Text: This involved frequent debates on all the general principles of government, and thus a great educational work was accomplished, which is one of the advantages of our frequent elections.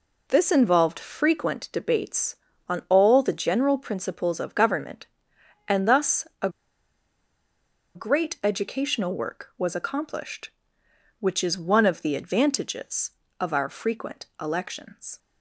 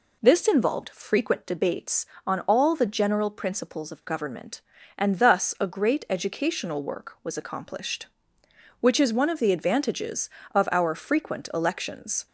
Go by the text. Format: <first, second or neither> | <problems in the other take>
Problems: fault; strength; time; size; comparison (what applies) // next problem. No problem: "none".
second | pauses between "a" and "great"; strong; at 6.4 s; 1.4 s long // pauses between "frequent" and "elections"; slight; at 14.2 s; 0.16 s long